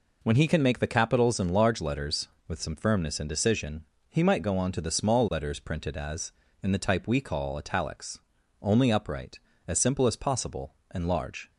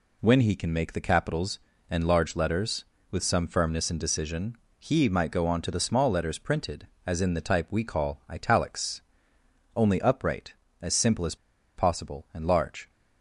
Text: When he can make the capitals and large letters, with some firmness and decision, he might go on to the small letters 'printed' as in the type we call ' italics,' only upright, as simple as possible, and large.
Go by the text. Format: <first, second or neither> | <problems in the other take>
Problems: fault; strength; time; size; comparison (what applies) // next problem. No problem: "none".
first | pauses between "as" and "possible"; at 11.3 s; 0.41 s long